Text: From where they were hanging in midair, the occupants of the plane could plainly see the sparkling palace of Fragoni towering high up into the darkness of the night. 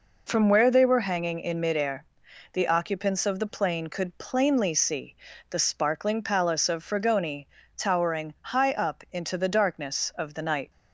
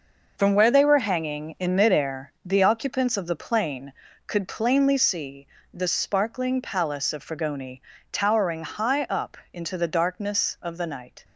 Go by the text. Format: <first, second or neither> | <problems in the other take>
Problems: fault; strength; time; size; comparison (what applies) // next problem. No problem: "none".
first | gets quieter; strong; throughout; 9.5 dB // pauses between "see" and "the"; slight; at 5.4 s; 0.26 s long; slight in the first // pauses between "Fragoni" and "towering"; slight; at 7.8 s; 0.32 s long; slight in the first // pauses between "up" and "into"; slight; at 9.3 s; 0.16 s long